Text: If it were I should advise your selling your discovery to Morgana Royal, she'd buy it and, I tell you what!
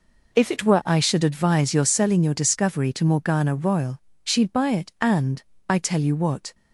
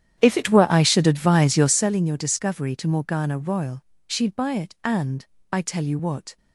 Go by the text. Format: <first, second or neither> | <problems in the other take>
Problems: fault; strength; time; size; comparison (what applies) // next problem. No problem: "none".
first | starts louder than the rest; strong; until 2.0 s; 10 dB